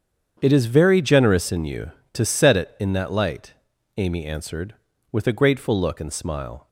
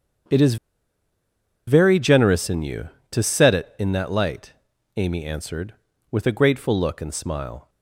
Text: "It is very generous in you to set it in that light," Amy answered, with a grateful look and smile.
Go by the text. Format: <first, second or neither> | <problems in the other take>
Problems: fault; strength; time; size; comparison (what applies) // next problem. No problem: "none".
first | starts louder than the rest; strong; until 2.4 s; 8 dB; strong in the first // pauses between "is" and "very"; at 0.5 s; 1.1 s long